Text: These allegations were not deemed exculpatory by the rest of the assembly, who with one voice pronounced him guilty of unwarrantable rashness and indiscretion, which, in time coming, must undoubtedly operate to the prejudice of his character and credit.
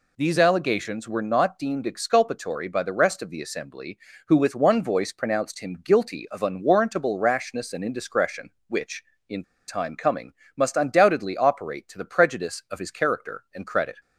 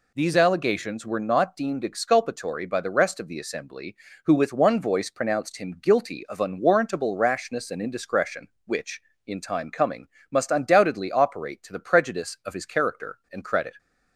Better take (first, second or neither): second